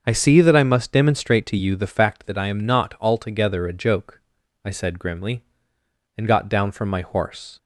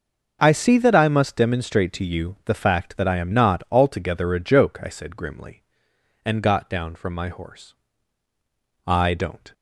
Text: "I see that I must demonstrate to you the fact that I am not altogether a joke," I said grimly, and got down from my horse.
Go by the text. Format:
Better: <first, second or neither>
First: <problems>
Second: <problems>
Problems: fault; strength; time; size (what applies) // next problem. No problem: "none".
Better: first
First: starts louder than the rest; until 1.0 s; 7 dB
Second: starts louder than the rest; noticeable; until 1.4 s; 6 dB // goes on to say "I don't"; noticeable; from 8.8 s on; 0.66 s long